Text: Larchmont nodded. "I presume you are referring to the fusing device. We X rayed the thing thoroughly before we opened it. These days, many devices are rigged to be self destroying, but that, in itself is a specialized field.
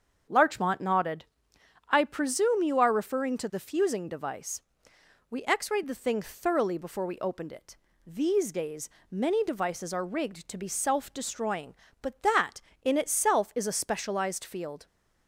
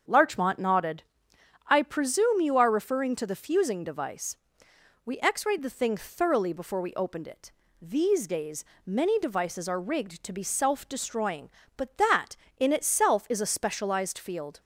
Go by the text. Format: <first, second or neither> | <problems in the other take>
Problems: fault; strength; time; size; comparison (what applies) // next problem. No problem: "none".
neither | starts louder than the rest; strong; the same in both